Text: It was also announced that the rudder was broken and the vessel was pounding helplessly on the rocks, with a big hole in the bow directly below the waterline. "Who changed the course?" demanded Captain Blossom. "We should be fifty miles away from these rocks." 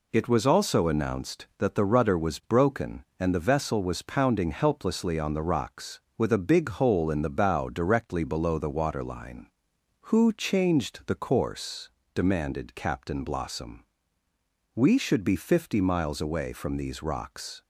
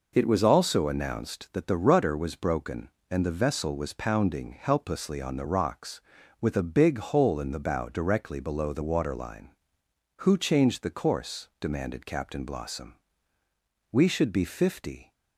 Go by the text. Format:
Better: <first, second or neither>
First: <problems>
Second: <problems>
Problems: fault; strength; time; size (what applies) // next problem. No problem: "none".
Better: first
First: none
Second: stops before "miles away from these rocks"; at 15.1 s